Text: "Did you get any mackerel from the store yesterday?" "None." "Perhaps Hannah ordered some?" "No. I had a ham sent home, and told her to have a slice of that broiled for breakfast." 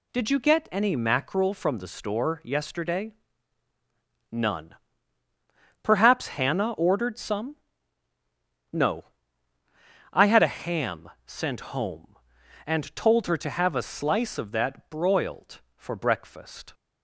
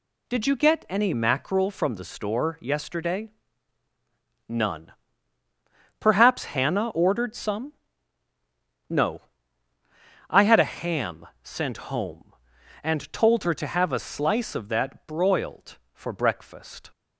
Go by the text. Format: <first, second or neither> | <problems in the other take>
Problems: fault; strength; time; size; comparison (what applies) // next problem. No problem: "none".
neither | pauses between "ham" and "sent"; slight; the same in both